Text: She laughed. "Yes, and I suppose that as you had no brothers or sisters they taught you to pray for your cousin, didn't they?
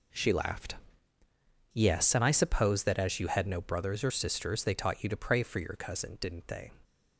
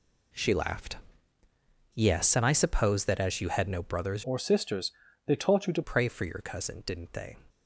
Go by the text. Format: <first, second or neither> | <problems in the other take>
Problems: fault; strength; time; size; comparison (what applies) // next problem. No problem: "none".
first | changes voice from "or" to "to"; from 4.2 to 5.8 s; 1.6 s long // pauses between "sisters" and "they"; slight; at 4.9 s; 0.34 s long